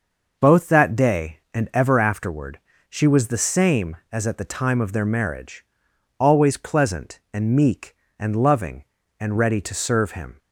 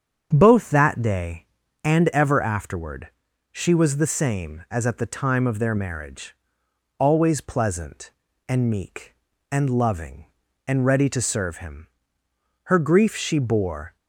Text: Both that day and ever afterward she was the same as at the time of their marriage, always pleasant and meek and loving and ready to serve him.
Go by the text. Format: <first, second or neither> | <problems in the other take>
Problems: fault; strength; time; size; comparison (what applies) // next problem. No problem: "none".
first | starts louder than the rest; strong; until 1.3 s; 7.5 dB // pauses between "afterward" and "she"; at 3.0 s; 0.42 s long; slight in the first // goes on to say "Her grief she bore"; noticeable; from 12.6 s on; 1.3 s long